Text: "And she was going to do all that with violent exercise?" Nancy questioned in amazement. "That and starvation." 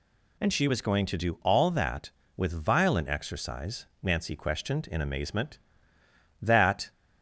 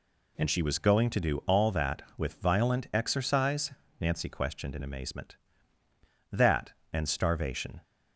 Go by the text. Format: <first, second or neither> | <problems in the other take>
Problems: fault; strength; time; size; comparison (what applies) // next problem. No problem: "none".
second | stops before "and starvation"; at 6.9 s